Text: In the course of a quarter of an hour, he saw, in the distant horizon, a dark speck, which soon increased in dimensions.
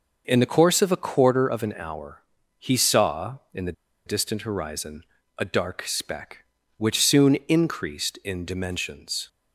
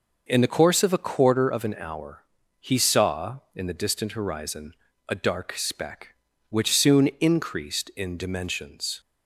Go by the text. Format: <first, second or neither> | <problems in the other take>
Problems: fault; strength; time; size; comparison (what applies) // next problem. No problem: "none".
second | pauses between "the" and "distant"; slight; at 3.7 s; 0.33 s long